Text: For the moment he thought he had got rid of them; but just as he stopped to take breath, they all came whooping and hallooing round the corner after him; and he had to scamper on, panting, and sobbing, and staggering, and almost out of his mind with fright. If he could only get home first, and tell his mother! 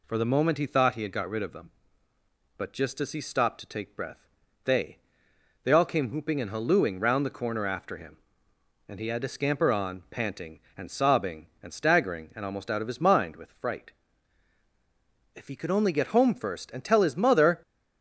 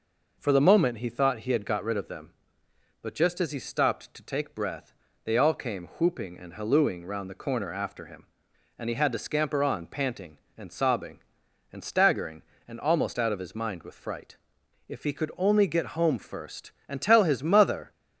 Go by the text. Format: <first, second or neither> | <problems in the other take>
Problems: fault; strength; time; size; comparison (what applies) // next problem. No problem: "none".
second | says "they" twice; at 5.6 s